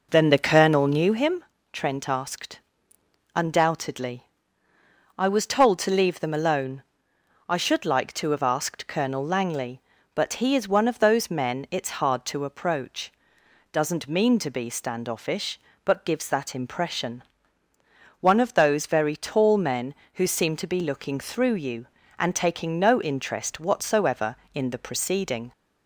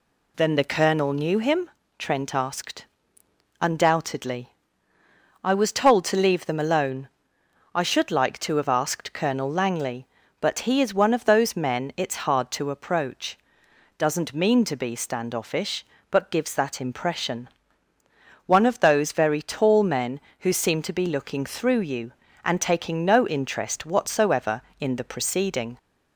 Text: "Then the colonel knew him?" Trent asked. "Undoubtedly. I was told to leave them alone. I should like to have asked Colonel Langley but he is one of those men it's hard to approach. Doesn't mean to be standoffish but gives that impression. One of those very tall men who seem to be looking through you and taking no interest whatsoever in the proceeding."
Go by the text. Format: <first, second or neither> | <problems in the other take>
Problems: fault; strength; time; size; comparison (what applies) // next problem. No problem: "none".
second | starts louder than the rest; noticeable; until 1.2 s; 5 dB